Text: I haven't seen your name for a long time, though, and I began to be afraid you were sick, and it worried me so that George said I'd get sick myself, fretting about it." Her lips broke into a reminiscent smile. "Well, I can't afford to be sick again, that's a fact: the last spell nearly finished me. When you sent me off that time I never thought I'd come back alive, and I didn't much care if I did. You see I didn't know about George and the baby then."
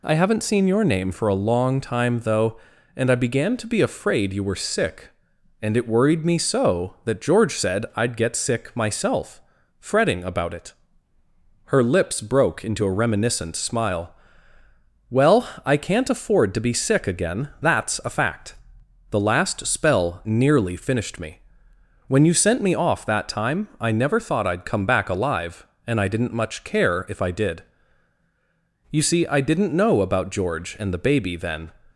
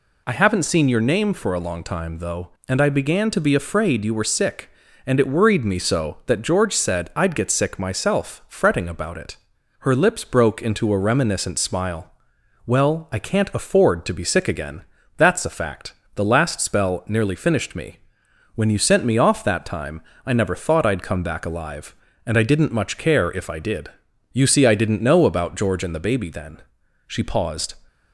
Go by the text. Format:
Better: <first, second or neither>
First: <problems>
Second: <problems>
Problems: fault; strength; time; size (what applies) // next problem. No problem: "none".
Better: first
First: none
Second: pauses between "time" and "I"; slight; at 20.0 s; 0.20 s long // goes on to say "She paused"; noticeable; from 27.0 s on; 0.68 s long